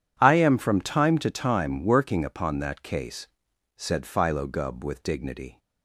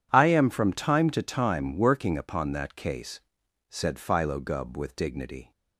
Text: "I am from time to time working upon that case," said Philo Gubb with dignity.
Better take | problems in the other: neither | none

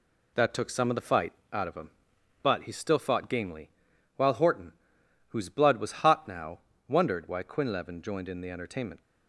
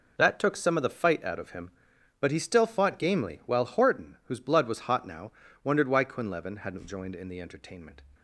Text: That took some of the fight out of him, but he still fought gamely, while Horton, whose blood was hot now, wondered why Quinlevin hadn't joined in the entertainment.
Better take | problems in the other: second | pauses between "fight" and "out"; slight; at 1.3 s; 0.18 s long // skips "hadn't"; at 8.0 s

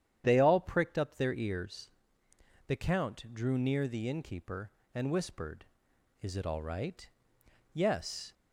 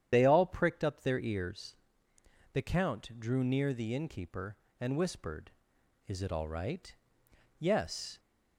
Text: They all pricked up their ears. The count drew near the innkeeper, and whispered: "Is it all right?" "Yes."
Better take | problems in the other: first | loses the start of "They"; at 0.1 s; 30 ms // starts louder than the rest; strong; until 1.1 s; 9.5 dB; strong in the first

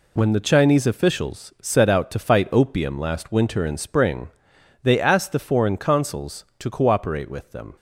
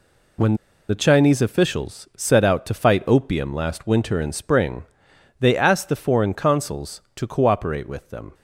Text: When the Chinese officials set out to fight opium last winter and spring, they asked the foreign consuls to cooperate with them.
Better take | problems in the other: first | pauses between "When" and "the"; slight; at 0.5 s; 0.33 s long

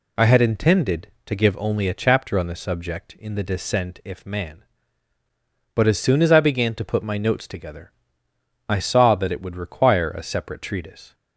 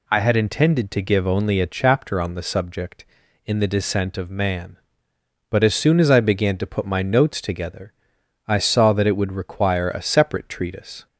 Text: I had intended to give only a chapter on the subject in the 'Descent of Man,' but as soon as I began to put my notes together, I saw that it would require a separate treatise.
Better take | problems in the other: second | says "if" for "of"; at 4.0 s

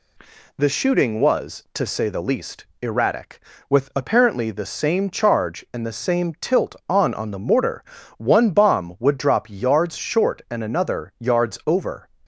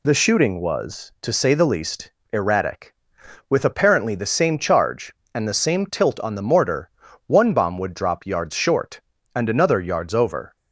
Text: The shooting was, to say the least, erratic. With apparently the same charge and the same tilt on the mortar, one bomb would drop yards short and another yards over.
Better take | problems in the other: second | says "on" twice; at 7.1 s

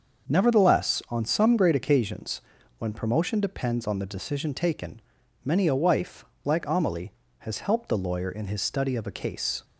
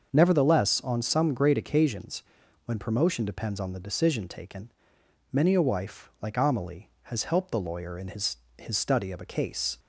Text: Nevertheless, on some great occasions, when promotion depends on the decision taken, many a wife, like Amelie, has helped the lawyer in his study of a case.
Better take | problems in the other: first | starts louder than the rest; until 1.1 s; 6.5 dB; also in the first // says "his" twice; at 8.5 s

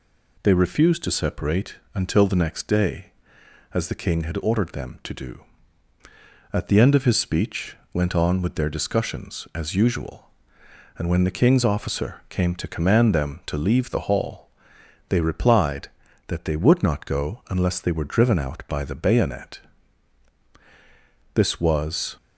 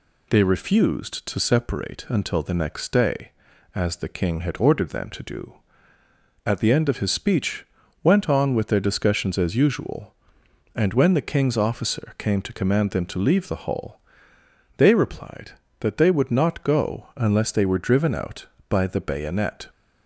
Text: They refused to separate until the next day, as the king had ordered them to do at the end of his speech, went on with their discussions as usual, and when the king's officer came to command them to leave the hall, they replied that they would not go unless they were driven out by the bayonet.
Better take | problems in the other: second | pauses between "separate" and "until"; slight; at 1.7 s; 0.18 s long // goes on to say "This was"; noticeable; from 21.3 s on; 0.82 s long

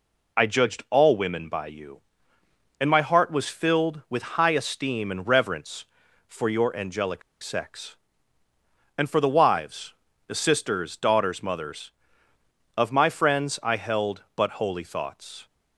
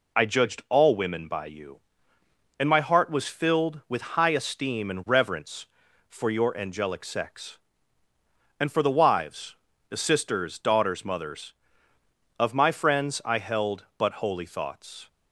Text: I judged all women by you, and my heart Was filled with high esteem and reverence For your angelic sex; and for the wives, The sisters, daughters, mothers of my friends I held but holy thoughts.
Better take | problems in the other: second | pauses between "angelic" and "sex"; slight; at 7.2 s; 0.21 s long

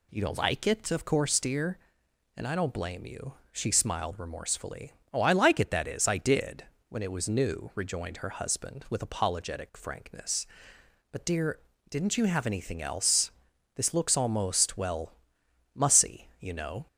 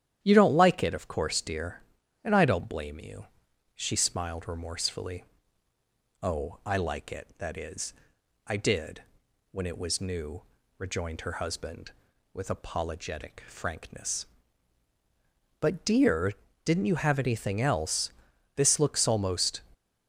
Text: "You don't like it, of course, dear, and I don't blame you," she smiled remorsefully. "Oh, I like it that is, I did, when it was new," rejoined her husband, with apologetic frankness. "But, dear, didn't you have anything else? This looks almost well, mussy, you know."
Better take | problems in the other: first | starts louder than the rest; strong; until 1.2 s; 10.5 dB // stops before "well mussy you know"; at 19.7 s

